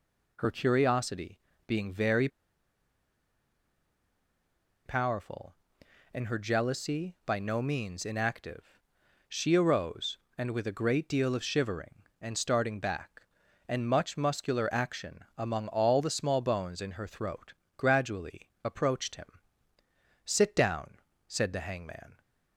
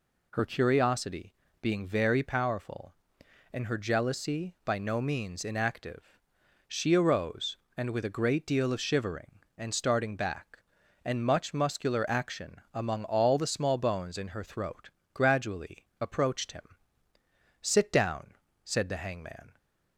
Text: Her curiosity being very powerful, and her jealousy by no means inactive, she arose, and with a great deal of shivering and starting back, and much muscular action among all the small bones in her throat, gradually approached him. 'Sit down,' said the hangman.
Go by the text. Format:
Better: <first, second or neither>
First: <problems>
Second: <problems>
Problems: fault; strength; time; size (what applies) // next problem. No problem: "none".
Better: second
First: pauses between "curiosity" and "being"; slight; at 1.3 s; 0.26 s long // pauses between "very" and "powerful"; strong; at 2.2 s; 2.5 s long // pauses between "gradually" and "approached"; slight; at 18.4 s; 0.16 s long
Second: pauses between "curiosity" and "being"; slight; at 1.3 s; 0.26 s long // pauses between "gradually" and "approached"; slight; at 15.8 s; 0.16 s long